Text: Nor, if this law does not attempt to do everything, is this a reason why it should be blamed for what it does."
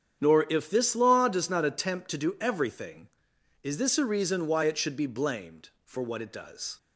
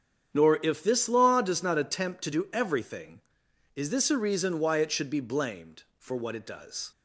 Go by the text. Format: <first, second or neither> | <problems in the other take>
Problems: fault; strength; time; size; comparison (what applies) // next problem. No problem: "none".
neither | starts louder than the rest; strong; the same in both